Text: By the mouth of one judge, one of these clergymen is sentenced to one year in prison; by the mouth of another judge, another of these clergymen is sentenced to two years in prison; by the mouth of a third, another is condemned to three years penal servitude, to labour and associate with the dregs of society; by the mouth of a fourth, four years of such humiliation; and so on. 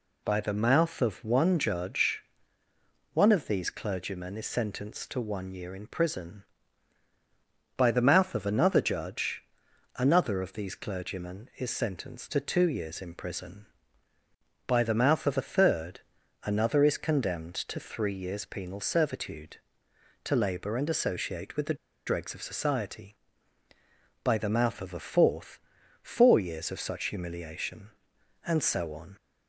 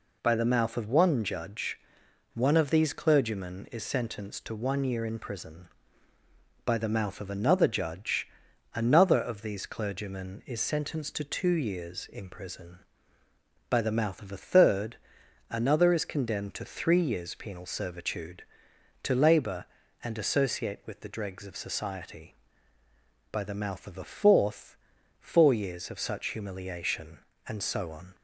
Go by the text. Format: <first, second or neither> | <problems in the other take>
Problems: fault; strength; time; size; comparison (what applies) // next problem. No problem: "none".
second | pauses between "the" and "dregs"; slight; at 21.7 s; 0.31 s long